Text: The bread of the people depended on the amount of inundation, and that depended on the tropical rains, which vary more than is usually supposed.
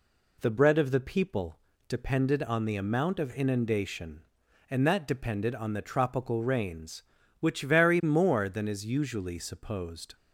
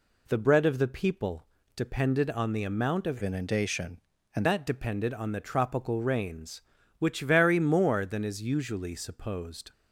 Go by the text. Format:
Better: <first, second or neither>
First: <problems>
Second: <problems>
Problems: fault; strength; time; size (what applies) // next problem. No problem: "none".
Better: first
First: pauses between "people" and "depended"; slight; at 1.5 s; 0.30 s long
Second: pauses between "people" and "depended"; slight; at 1.4 s; 0.30 s long // changes voice from "inundation" to "and"; from 3.2 to 4.4 s; 1.2 s long